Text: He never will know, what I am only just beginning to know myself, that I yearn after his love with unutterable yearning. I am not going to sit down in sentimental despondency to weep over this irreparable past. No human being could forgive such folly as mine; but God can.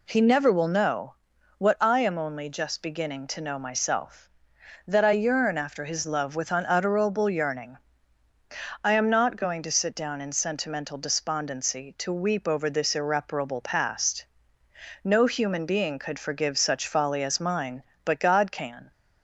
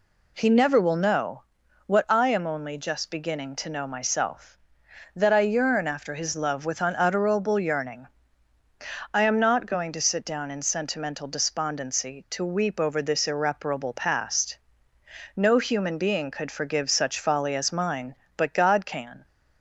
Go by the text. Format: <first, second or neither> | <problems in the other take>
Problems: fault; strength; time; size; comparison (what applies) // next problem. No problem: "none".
neither | none